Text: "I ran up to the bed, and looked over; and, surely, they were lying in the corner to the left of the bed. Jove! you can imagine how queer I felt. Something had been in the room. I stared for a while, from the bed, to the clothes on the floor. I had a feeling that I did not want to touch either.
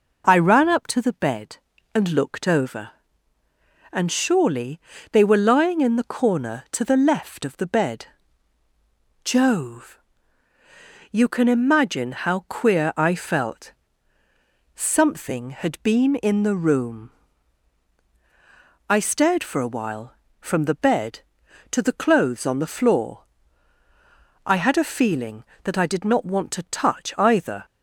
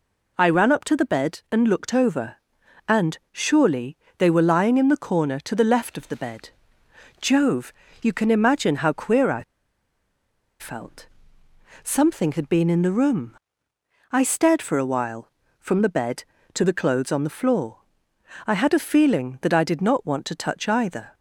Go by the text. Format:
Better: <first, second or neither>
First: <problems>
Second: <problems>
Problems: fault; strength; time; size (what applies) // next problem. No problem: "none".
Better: first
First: none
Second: pauses between "I" and "felt"; at 9.4 s; 1.1 s long